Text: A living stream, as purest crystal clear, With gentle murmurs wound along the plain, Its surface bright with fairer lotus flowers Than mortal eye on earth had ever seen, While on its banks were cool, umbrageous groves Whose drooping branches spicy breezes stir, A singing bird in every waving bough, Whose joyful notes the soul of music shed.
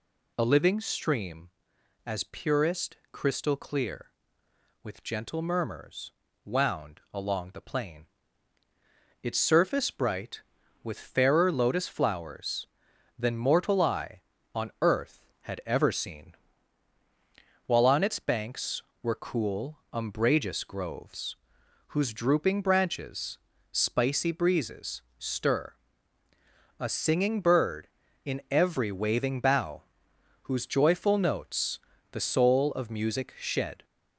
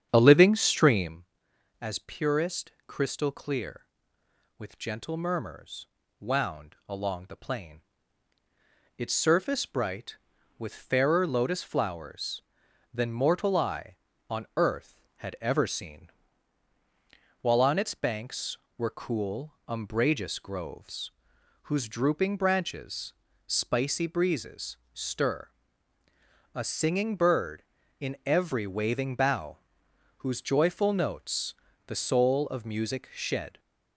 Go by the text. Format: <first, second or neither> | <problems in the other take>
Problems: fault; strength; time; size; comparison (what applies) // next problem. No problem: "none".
first | starts louder than the rest; strong; until 1.2 s; 8.5 dB // pauses between "purest" and "crystal"; slight; at 2.7 s; 0.16 s long; slight in the first // pauses between "murmurs" and "wound"; slight; at 5.8 s; 0.34 s long; slight in the first // pauses between "groves" and "Whose"; noticeable; at 21.1 s; 0.54 s long; noticeable in the first // pauses between "branches" and "spicy"; slight; at 23.1 s; 0.32 s long; slight in the first // pauses between "breezes" and "stir"; slight; at 24.7 s; 0.16 s long; slight in the first // pauses between "notes" and "the"; slight; at 31.5 s; 0.34 s long; slight in the first